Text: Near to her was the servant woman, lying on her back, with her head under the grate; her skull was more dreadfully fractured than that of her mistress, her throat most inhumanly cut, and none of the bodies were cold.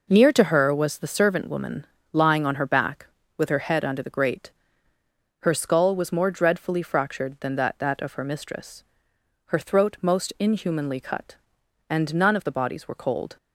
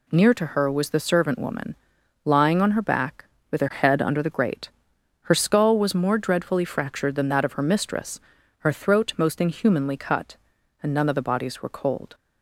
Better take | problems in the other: second | says "that" twice; at 7.7 s

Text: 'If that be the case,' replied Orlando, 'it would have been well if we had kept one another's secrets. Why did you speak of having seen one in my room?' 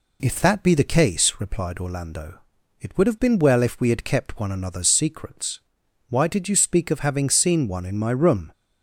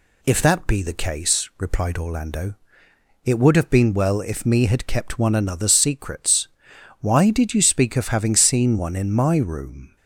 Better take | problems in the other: first | says "me" for "we"; at 4.4 s

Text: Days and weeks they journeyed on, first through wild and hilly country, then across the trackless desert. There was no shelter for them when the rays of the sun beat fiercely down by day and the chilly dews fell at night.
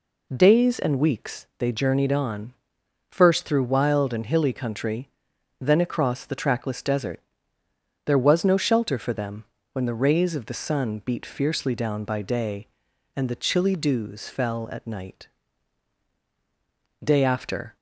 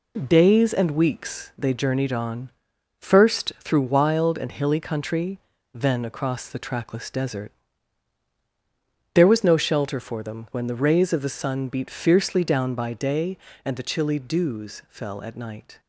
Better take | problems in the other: second | pauses between "them" and "when"; slight; at 9.4 s; 0.28 s long // goes on to say "Day after"; noticeable; from 17.0 s on; 0.72 s long

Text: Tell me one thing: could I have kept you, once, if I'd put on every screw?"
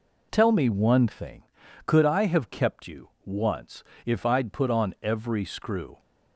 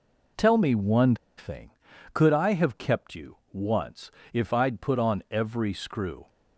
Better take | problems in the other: first | pauses between "one" and "thing"; slight; at 1.1 s; 0.21 s long

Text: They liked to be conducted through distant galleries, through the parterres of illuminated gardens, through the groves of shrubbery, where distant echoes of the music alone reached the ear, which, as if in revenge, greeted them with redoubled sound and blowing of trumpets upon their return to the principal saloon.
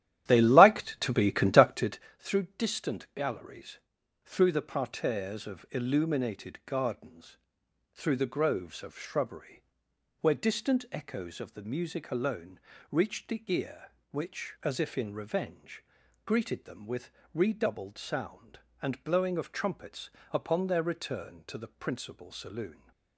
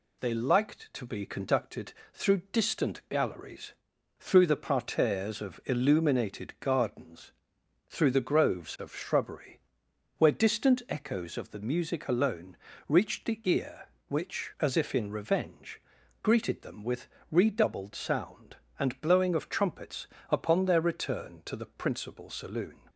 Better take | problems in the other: second | starts louder than the rest; strong; until 2.1 s; 12 dB // pauses between "conducted" and "through"; slight; at 1.9 s; 0.22 s long; slight in the second // pauses between "alone" and "reached"; slight; at 12.6 s; 0.32 s long; slight in the second // pauses between "with" and "redoubled"; slight; at 17.1 s; 0.24 s long; slight in the second // pauses between "trumpets" and "upon"; slight; at 20.0 s; 0.22 s long; slight in the second

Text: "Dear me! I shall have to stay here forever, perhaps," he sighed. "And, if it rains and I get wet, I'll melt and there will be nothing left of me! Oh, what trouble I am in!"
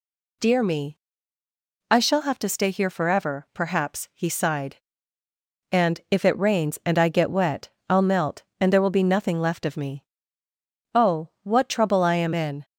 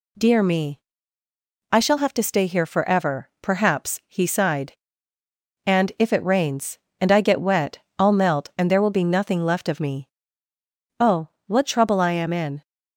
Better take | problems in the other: neither | none

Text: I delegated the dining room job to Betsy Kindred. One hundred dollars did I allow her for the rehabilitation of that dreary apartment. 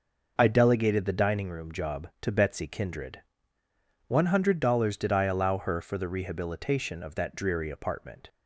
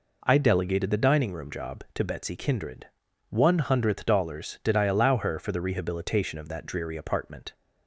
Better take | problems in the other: first | says "hundredth" for "hundred"; at 3.5 s

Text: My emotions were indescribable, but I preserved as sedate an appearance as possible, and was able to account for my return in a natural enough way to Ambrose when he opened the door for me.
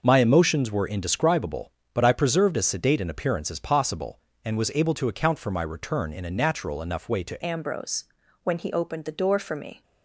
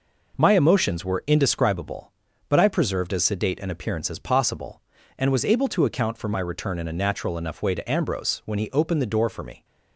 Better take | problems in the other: second | changes voice at "Ambrose"; from 7.4 s on; 2.4 s long // pauses between "Ambrose" and "when"; at 8.0 s; 0.40 s long

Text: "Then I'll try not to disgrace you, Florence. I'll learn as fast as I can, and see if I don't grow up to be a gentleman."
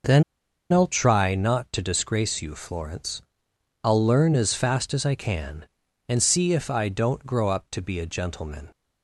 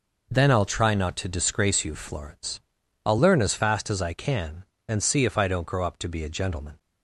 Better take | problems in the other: second | pauses between "Then" and "I'll"; noticeable; at 0.2 s; 0.47 s long

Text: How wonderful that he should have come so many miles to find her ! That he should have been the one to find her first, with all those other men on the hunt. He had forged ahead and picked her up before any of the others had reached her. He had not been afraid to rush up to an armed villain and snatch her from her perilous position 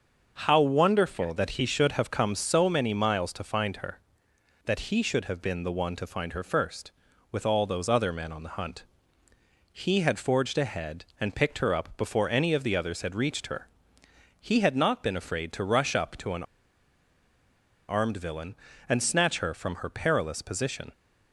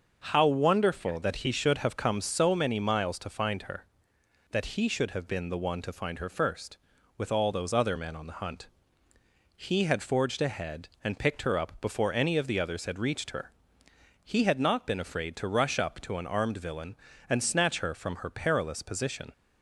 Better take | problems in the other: second | starts louder than the rest; until 1.4 s; 6.5 dB; also in the second // pauses between "an" and "armed"; strong; at 16.4 s; 1.4 s long

